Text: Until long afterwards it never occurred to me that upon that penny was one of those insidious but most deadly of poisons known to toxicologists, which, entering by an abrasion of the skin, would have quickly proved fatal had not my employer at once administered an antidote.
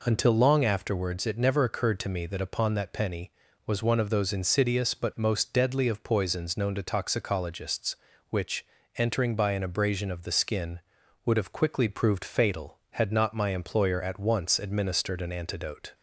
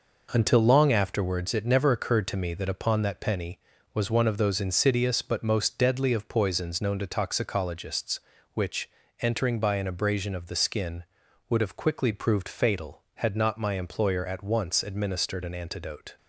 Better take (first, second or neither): first